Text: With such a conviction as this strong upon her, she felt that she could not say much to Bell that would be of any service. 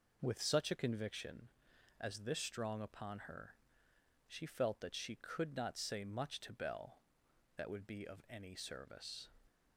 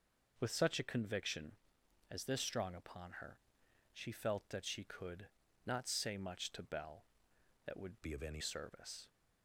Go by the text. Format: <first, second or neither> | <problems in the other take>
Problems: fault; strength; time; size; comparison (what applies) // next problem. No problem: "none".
first | pauses between "could" and "not"; at 5.2 s; 0.38 s long // changes voice from "be" to "any"; from 8.0 to 8.4 s; 0.4 s long